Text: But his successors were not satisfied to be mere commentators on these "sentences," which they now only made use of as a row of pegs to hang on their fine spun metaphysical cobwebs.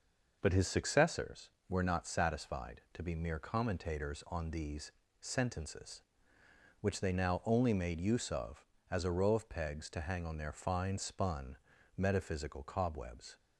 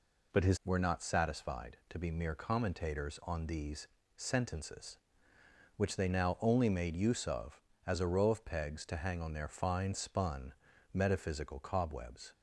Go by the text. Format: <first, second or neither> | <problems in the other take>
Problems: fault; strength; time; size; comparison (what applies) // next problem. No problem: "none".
first | skips "successors"; at 0.6 s // pauses between "these" and "sentences"; slight; at 3.8 s; 0.30 s long; slight in the first // pauses between "spun" and "metaphysical"; at 10.5 s; 0.40 s long; also in the first